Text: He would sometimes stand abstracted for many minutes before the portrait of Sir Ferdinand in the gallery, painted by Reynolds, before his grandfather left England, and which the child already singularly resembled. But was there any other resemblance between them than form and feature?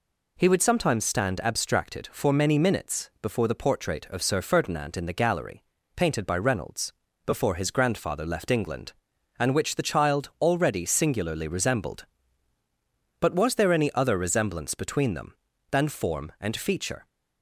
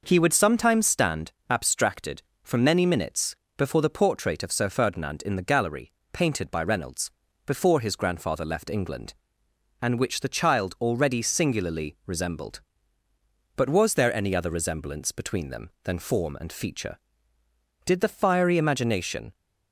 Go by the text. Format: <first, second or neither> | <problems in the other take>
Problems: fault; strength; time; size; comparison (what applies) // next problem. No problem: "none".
first | pauses between "stand" and "abstracted"; slight; at 1.3 s; 0.16 s long // pauses between "minutes" and "before"; slight; at 3.3 s; 0.22 s long // goes on to say "Did the fiery imagination"; from 17.8 s on; 1.5 s long